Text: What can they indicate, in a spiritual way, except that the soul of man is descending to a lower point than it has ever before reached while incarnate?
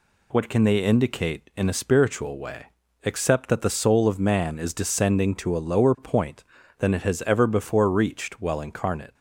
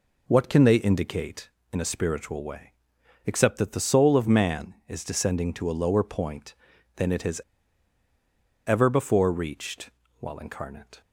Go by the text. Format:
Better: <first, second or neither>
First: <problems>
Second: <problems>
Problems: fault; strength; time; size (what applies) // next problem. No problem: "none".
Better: first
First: none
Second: pauses between "has" and "ever"; strong; at 7.4 s; 1.2 s long // pauses between "reached" and "while"; slight; at 9.8 s; 0.30 s long